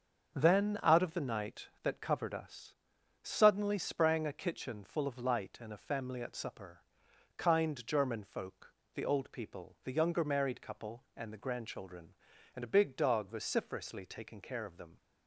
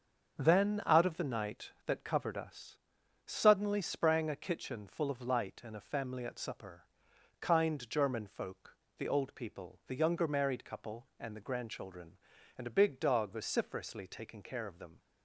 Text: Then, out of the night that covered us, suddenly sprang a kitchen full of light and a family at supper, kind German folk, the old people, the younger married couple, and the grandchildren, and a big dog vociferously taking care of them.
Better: neither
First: starts louder than the rest; until 1.3 s; 6.5 dB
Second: starts louder than the rest; until 1.4 s; 7 dB

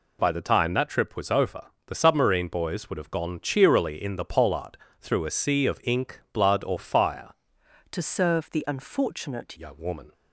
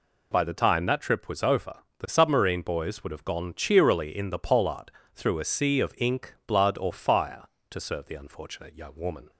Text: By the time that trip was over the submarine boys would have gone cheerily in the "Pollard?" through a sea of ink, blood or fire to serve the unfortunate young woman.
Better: second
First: pauses between "over" and "the"; slight; at 1.6 s; 0.24 s long // changes voice from "to" to "unfortunate"; from 7.9 to 9.5 s; 1.6 s long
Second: pauses between "over" and "the"; slight; at 1.7 s; 0.24 s long

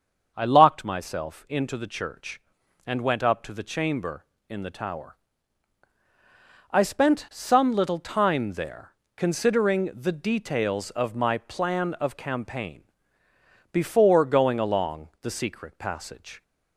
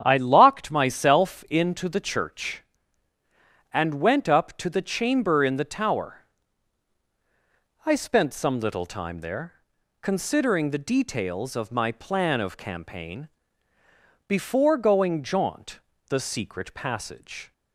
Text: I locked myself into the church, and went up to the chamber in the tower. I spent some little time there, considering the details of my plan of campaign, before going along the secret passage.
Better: first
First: starts louder than the rest; until 1.3 s; 6.5 dB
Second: starts louder than the rest; strong; until 1.0 s; 8.5 dB // says "jaunt" for "along"; at 15.2 s

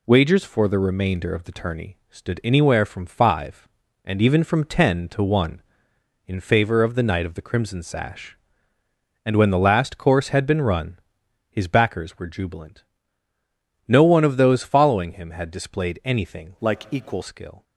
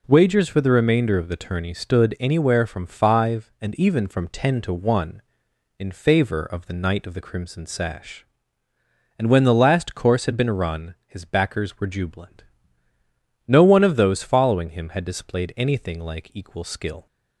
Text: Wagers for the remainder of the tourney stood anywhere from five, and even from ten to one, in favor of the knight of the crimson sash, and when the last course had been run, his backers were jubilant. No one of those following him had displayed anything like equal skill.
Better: second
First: changes voice from "like" to "equal"; from 16.6 to 17.2 s; 0.6 s long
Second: none

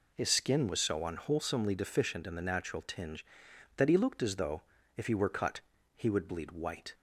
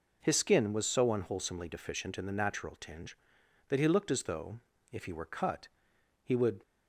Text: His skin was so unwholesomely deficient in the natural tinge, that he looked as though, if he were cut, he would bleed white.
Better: first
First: none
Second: stops before "bleed white"; at 6.6 s

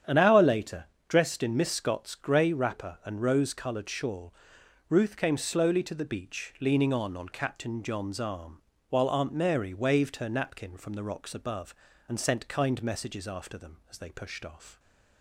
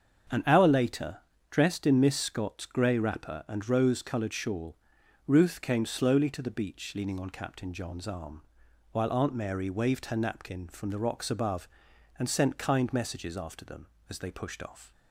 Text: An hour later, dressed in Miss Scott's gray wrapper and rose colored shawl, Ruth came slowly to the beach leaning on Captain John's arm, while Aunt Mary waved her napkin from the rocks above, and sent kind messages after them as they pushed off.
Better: second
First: starts louder than the rest; strong; until 1.3 s; 9 dB // says "on" twice; at 7.1 s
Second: starts louder than the rest; strong; until 1.6 s; 7.5 dB

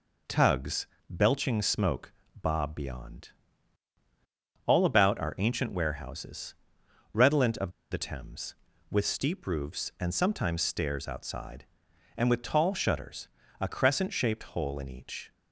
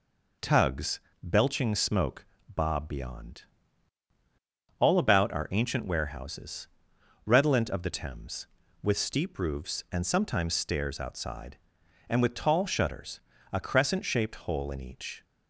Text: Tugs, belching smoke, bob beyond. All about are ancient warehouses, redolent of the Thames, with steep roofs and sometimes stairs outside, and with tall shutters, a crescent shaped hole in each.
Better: second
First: pauses between "of" and "the"; slight; at 7.6 s; 0.21 s long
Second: none

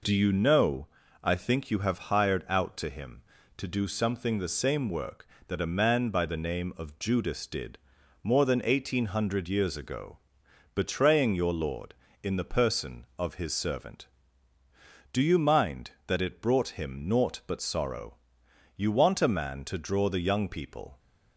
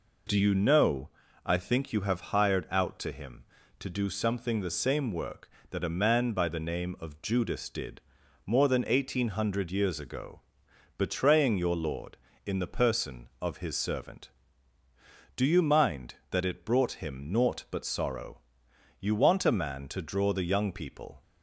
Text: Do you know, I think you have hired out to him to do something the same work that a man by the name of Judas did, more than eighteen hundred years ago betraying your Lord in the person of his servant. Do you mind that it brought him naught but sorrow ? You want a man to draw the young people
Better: neither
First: pauses between "ago" and "betraying"; noticeable; at 10.1 s; 0.58 s long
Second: pauses between "ago" and "betraying"; noticeable; at 10.3 s; 0.58 s long

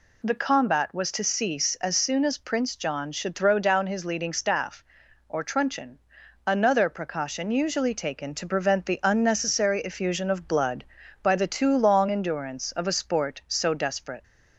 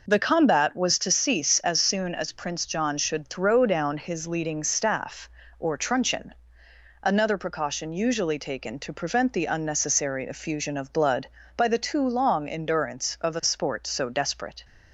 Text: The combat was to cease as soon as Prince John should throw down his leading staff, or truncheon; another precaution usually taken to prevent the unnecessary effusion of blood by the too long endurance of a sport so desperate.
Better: neither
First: none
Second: none

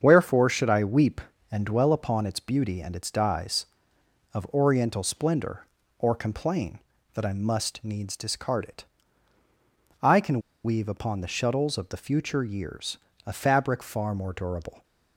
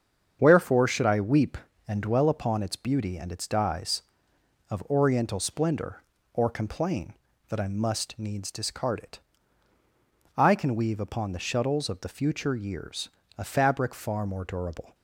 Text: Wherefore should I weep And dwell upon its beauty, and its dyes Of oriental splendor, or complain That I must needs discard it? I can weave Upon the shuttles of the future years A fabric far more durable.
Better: second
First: starts louder than the rest; strong; until 1.0 s; 7 dB // pauses between "can" and "weave"; slight; at 10.4 s; 0.24 s long // pauses between "years" and "A"; slight; at 12.9 s; 0.30 s long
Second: starts louder than the rest; strong; until 1.4 s; 7 dB // pauses between "years" and "A"; slight; at 13.0 s; 0.30 s long

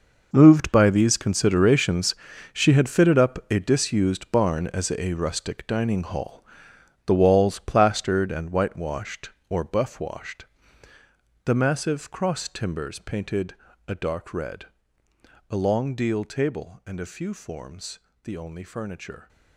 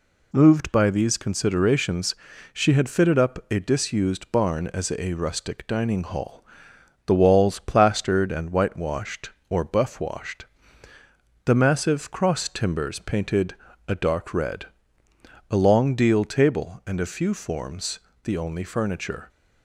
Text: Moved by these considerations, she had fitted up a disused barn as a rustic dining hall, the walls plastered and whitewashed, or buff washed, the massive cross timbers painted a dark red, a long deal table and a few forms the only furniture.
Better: second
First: gets quieter; strong; throughout; 13.5 dB // pauses between "painted" and "a"; slight; at 13.5 s; 0.32 s long // pauses between "forms" and "the"; slight; at 17.9 s; 0.26 s long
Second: pauses between "painted" and "a"; slight; at 13.5 s; 0.32 s long // pauses between "forms" and "the"; slight; at 17.9 s; 0.26 s long

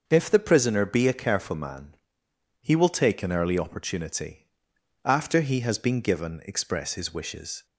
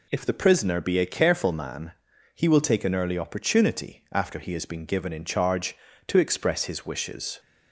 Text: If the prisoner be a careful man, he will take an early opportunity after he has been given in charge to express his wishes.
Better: second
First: starts louder than the rest; until 1.0 s; 6.5 dB // pauses between "opportunity" and "after"; noticeable; at 4.4 s; 0.58 s long // skips "in charge to"; at 6.4 s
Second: none

